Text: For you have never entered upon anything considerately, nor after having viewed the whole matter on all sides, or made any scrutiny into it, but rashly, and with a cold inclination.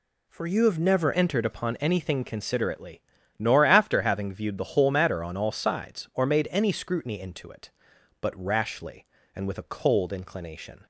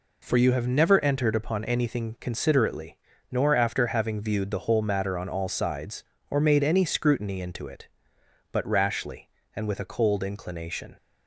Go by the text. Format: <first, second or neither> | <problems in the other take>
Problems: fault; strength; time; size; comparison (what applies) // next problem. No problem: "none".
second | changes voice at "entered"; from 1.1 s on; 9.7 s long